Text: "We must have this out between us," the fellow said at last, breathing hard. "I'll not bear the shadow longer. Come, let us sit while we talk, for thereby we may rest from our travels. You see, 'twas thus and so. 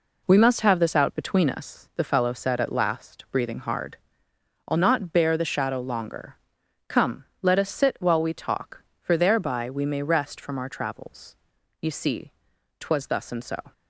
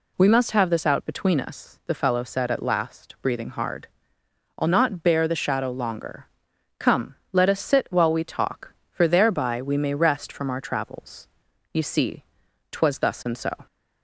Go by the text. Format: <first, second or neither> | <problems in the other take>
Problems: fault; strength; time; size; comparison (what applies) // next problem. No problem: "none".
second | gets quieter; strong; throughout; 7 dB